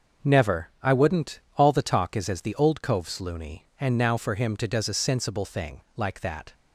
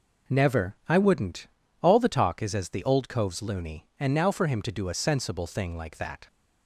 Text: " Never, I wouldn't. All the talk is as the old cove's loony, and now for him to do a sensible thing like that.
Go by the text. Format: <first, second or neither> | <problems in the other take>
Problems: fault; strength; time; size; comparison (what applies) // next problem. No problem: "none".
second | starts louder than the rest; noticeable; until 1.3 s; 6 dB // says "does" for "do"; at 4.6 s // pauses between "thing" and "like"; slight; at 5.8 s; 0.16 s long